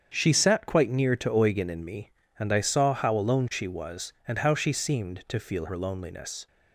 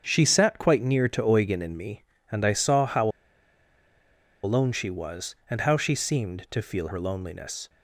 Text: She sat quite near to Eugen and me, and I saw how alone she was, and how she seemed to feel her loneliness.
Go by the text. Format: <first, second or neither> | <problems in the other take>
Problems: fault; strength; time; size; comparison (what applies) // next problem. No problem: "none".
first | starts louder than the rest; strong; until 1.0 s; 8 dB; strong in the first // pauses between "how" and "alone"; strong; at 3.0 s; 1.3 s long